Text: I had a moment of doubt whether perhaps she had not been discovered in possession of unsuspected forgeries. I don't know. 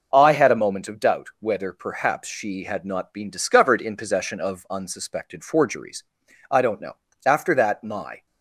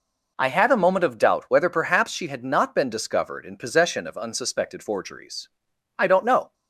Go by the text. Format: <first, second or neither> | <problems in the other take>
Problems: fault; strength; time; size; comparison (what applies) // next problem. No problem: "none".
second | goes on to say "After that my"; noticeable; from 7.2 s on; 1.0 s long